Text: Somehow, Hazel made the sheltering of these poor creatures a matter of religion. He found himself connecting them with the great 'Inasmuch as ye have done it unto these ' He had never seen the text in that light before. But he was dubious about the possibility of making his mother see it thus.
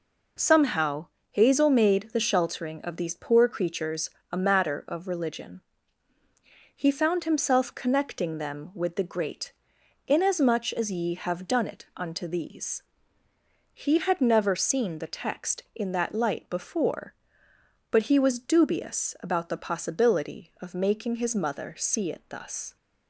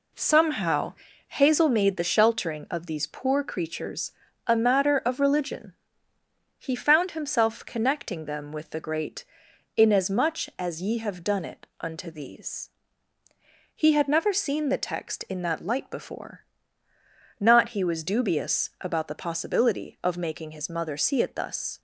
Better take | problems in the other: first | pauses between "creatures" and "a"; slight; at 4.1 s; 0.34 s long; slight in the first // pauses between "great" and "Inasmuch"; noticeable; at 9.2 s; 0.52 s long; noticeable in the first // says "Not" for "But"; at 17.4 s

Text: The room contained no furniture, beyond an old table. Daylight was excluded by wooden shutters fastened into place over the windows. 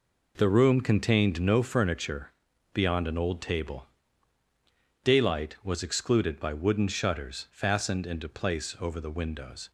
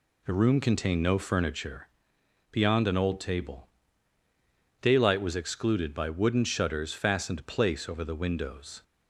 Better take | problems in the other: first | skips "into"; at 7.4 s

